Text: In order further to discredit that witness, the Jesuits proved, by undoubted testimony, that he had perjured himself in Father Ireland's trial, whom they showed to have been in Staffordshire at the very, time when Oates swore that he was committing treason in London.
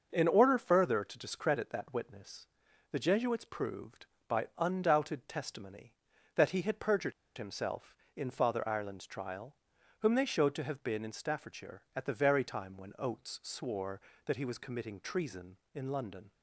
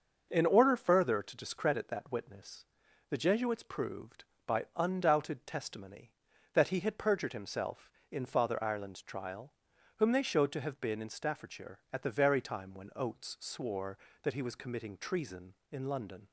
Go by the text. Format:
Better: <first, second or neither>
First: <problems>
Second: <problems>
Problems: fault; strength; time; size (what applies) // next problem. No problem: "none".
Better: second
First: starts louder than the rest; until 1.1 s; 6 dB // pauses between "perjured" and "himself"; slight; at 7.1 s; 0.25 s long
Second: starts louder than the rest; until 1.3 s; 6 dB